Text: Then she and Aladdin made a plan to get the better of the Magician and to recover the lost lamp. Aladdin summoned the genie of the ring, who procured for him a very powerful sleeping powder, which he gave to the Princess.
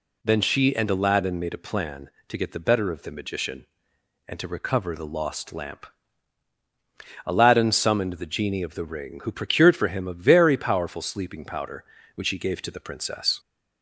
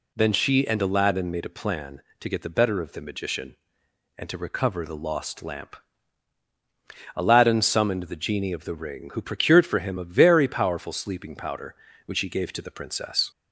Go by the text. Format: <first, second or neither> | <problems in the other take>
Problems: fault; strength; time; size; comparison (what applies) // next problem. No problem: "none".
neither | none